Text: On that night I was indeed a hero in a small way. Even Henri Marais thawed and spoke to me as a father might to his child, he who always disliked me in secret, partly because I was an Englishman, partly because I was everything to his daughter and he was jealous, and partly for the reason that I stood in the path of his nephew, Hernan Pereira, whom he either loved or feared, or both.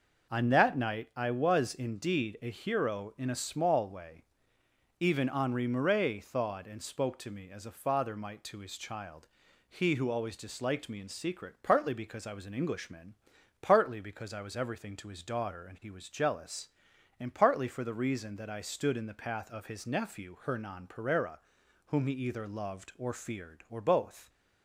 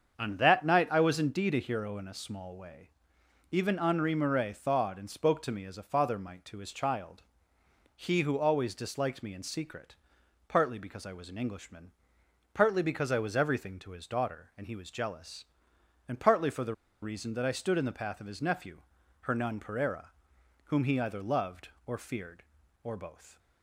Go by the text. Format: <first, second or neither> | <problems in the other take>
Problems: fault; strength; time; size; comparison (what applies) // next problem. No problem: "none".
first | starts louder than the rest; strong; until 1.2 s; 7 dB // pauses between "the" and "reason"; slight; at 16.7 s; 0.27 s long